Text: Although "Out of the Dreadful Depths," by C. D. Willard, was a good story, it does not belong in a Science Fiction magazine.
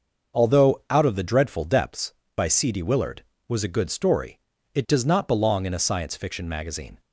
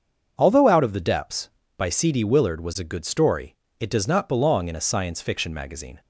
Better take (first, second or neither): first